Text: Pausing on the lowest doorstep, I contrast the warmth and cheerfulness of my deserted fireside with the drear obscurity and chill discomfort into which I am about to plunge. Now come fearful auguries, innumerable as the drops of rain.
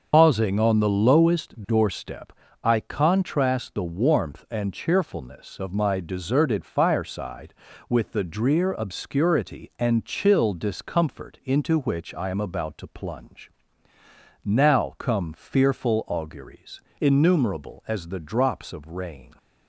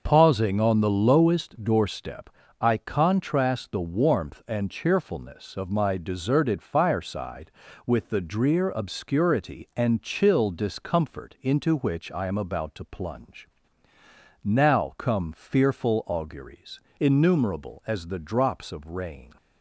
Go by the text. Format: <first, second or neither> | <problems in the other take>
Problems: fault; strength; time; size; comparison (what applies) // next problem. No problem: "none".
second | loses the start of "Pausing"; at 0.1 s; 90 ms // starts louder than the rest; until 1.1 s; 6.5 dB; noticeable in the second